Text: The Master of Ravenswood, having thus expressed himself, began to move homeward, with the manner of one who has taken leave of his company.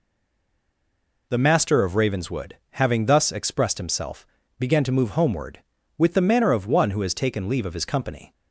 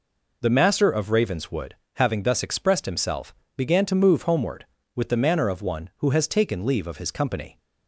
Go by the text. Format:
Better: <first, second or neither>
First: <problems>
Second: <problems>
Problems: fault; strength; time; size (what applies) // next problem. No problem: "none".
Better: second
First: stays silent before the first word; noticeable; until 1.2 s; 1.2 s long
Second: none